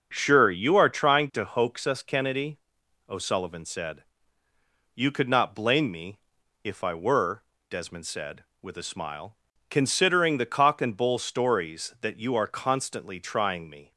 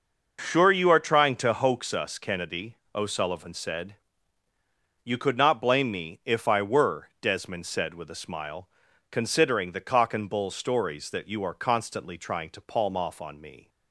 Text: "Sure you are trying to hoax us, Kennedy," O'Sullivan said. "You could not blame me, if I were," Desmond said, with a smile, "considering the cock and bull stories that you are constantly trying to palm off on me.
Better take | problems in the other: second | starts louder than the rest; noticeable; until 1.1 s; 6 dB // skips "to palm off on"; at 13.6 s

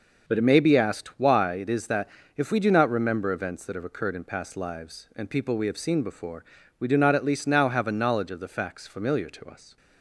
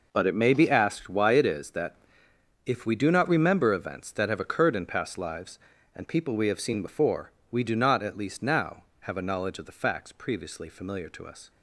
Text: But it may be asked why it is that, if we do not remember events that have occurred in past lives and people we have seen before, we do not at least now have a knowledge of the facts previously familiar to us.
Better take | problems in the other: second | skips "previously"; at 8.8 s

